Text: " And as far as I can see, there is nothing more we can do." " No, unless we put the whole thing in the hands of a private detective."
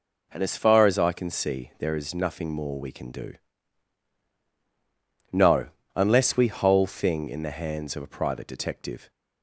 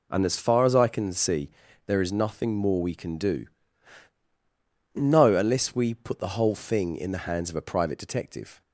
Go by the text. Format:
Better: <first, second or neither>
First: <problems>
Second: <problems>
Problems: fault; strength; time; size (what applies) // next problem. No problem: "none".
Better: second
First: skips "put the"; at 6.4 s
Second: none